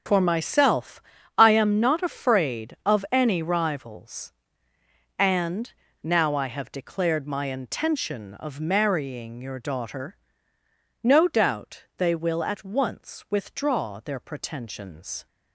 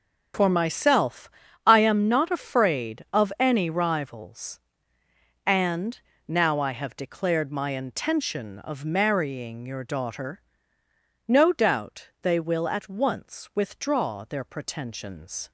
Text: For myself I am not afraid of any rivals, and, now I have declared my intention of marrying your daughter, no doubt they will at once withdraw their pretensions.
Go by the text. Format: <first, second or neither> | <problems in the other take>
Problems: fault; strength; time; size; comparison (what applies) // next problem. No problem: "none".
neither | starts louder than the rest; strong; the same in both // pauses between "myself" and "I"; slight; the same in both